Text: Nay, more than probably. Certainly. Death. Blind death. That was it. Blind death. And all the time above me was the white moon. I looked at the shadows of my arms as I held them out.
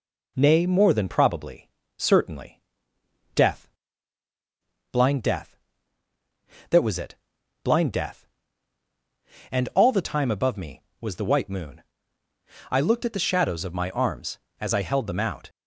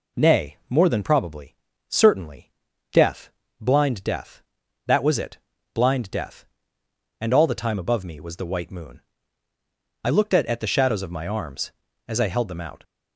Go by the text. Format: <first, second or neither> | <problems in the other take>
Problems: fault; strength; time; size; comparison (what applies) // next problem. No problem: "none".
first | says "at" twice; at 10.4 s